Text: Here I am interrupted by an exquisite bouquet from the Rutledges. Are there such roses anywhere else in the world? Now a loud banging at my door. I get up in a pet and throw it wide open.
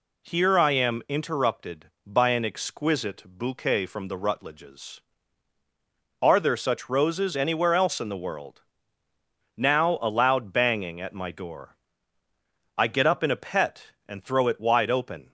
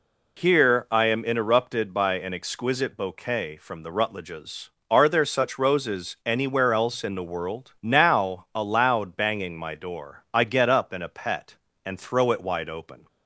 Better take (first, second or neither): first